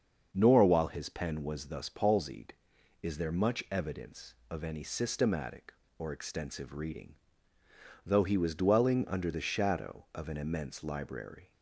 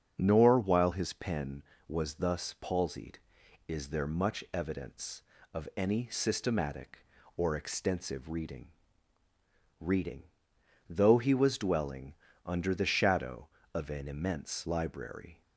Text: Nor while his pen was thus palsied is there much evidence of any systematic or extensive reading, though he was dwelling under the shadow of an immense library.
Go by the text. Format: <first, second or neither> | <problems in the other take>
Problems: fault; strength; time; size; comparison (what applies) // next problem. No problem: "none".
first | starts louder than the rest; until 1.1 s; 7 dB; also in the first // says "reading" twice; at 9.7 s // pauses between "dwelling" and "under"; slight; at 12.1 s; 0.32 s long